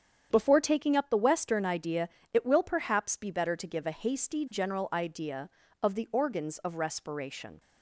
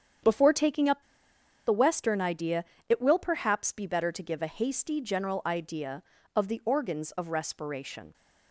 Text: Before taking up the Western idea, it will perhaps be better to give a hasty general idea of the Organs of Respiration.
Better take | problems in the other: first | starts louder than the rest; strong; until 1.8 s; 8.5 dB; strong in the first // pauses between "up" and "the"; noticeable; at 1.0 s; 0.64 s long

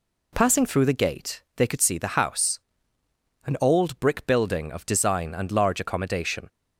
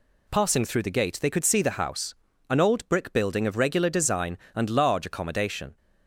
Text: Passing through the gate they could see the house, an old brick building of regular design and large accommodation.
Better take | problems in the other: second | skips "regular"; at 4.8 s

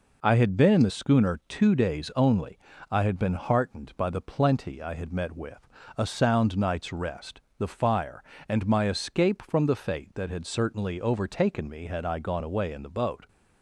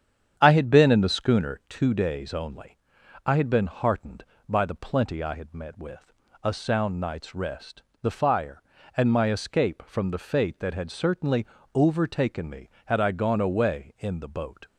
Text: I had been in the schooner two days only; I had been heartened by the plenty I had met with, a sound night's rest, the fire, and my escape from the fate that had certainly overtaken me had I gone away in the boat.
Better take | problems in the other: first | starts louder than the rest; strong; until 1.7 s; 8.5 dB // pauses between "certainly" and "overtaken"; slight; at 11.4 s; 0.26 s long

